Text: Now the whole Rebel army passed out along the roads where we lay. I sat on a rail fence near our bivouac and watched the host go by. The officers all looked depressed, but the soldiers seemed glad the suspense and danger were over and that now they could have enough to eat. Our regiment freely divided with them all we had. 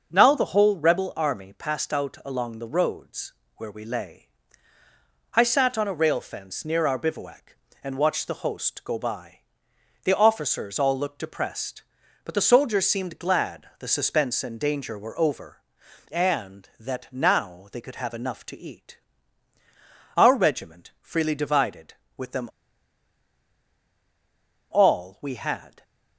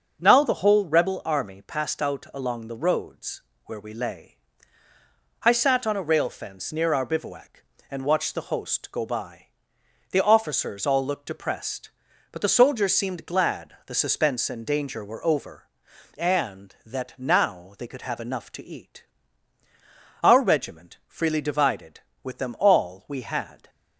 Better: second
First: starts louder than the rest; noticeable; until 1.1 s; 6 dB // pauses between "roads" and "where"; slight; at 3.3 s; 0.24 s long // pauses between "them" and "all"; strong; at 22.4 s; 2.2 s long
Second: starts louder than the rest; noticeable; until 1.2 s; 6 dB // pauses between "roads" and "where"; slight; at 3.3 s; 0.24 s long

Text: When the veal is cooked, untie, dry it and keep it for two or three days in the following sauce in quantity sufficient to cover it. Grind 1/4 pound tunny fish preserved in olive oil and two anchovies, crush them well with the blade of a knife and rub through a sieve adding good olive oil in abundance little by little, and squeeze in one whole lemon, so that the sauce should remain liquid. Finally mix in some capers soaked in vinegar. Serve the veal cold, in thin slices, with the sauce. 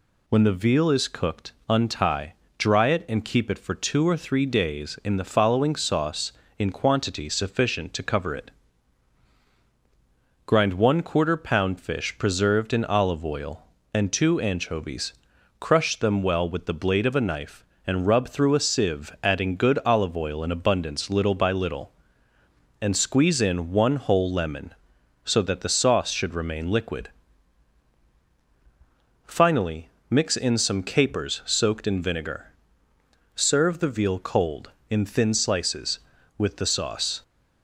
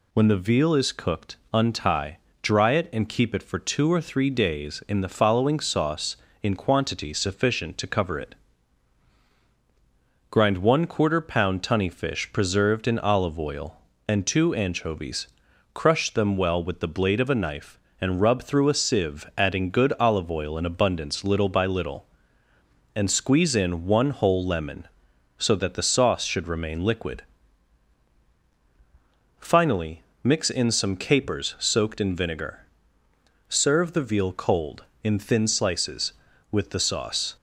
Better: second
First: skips "tunny"; at 11.7 s // pauses between "Finally" and "mix"; slight; at 29.8 s; 0.20 s long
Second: pauses between "Finally" and "mix"; slight; at 30.0 s; 0.20 s long

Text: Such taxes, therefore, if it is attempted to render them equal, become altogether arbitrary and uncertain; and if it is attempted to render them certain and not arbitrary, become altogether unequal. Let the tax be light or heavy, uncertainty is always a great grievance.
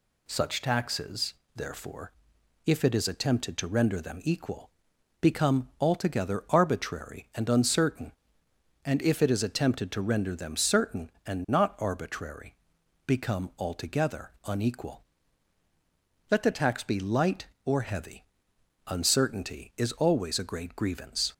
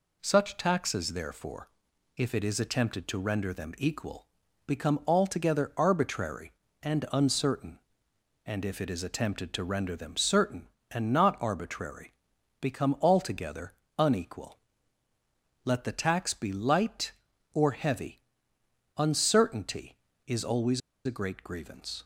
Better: first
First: none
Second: pauses between "altogether" and "unequal"; slight; at 13.7 s; 0.24 s long // pauses between "always" and "a"; slight; at 20.8 s; 0.27 s long

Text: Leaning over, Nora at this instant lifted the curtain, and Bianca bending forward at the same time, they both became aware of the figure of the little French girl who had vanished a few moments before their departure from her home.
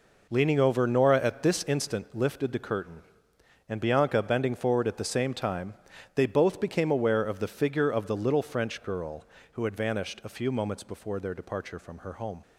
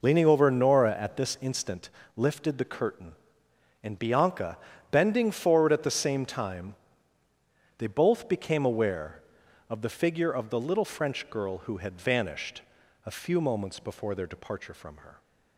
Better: first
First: none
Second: pauses between "instant" and "lifted"; slight; at 1.8 s; 0.28 s long // pauses between "Bianca" and "bending"; slight; at 4.5 s; 0.34 s long // pauses between "vanished" and "a"; at 12.6 s; 0.44 s long // stops before "home"; at 15.2 s

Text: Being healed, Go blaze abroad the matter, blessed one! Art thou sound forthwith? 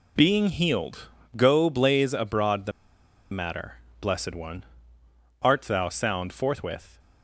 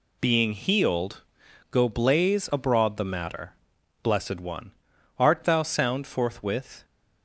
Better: second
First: pauses between "the" and "matter"; noticeable; at 2.7 s; 0.61 s long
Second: none

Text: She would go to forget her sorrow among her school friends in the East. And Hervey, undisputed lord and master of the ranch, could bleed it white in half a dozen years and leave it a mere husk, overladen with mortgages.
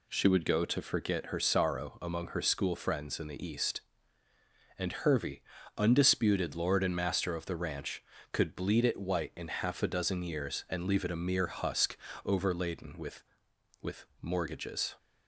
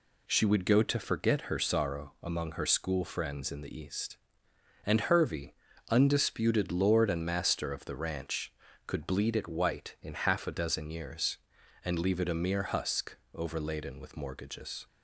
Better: second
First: says "with" twice; at 13.8 s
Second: none

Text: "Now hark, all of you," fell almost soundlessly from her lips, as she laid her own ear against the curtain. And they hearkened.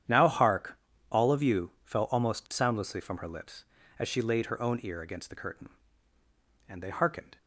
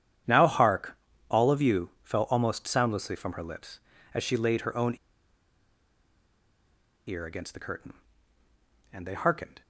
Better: first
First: starts louder than the rest; strong; until 1.4 s; 9.5 dB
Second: starts louder than the rest; strong; until 1.5 s; 9.5 dB // pauses between "own" and "ear"; strong; at 4.9 s; 2.1 s long

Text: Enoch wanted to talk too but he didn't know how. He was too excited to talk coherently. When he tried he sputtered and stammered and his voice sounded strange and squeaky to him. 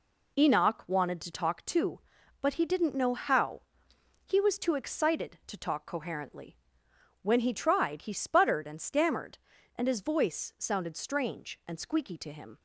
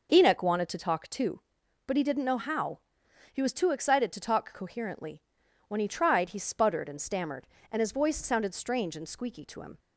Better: neither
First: none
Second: none

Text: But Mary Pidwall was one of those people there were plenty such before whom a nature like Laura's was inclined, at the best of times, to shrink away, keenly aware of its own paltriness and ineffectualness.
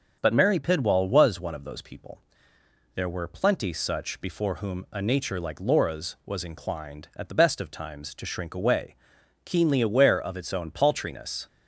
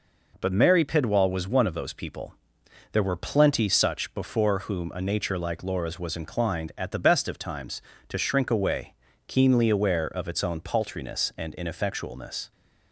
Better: second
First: starts louder than the rest; until 1.2 s; 6.5 dB // pauses between "people" and "there"; noticeable; at 2.2 s; 0.74 s long // stops before "and ineffectualness"; at 11.4 s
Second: pauses between "people" and "there"; noticeable; at 2.3 s; 0.58 s long

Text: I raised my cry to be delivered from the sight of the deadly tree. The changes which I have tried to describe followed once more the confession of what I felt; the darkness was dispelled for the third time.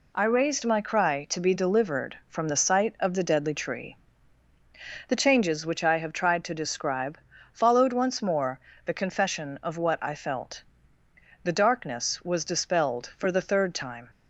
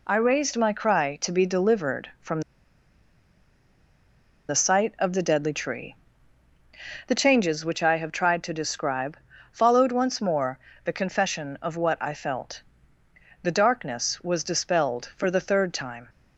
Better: first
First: pauses between "describe" and "followed"; slight; at 7.1 s; 0.34 s long // pauses between "more" and "the"; slight; at 8.5 s; 0.28 s long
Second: pauses between "from" and "the"; strong; at 2.4 s; 2.0 s long // pauses between "describe" and "followed"; slight; at 9.1 s; 0.34 s long // pauses between "more" and "the"; slight; at 10.5 s; 0.28 s long

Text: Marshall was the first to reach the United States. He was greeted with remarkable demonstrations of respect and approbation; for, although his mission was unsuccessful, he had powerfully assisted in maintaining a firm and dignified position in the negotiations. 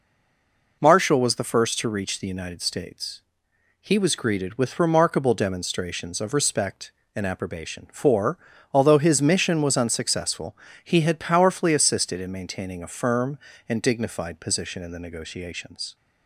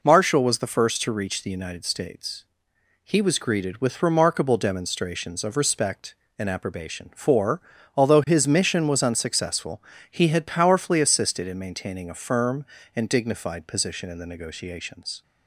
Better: second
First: stays silent before the first word; slight; until 0.8 s; 0.8 s long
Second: none

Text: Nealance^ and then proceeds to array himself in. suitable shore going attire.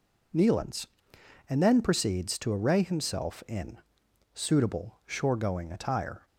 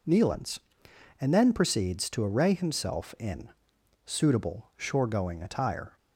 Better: neither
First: none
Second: none

